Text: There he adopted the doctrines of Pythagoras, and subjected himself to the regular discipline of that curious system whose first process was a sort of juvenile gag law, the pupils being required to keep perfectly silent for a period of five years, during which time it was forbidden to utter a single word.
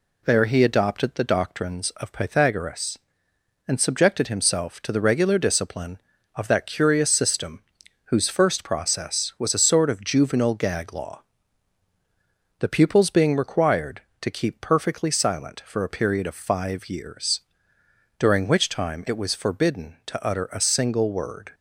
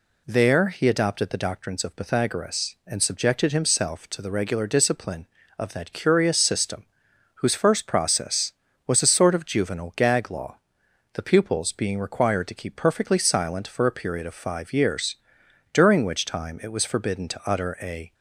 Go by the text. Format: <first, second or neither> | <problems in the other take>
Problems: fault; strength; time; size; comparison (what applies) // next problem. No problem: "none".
first | pauses between "system" and "whose"; noticeable; at 6.8 s; 0.50 s long; also in the first // stops before "single word"; at 18.1 s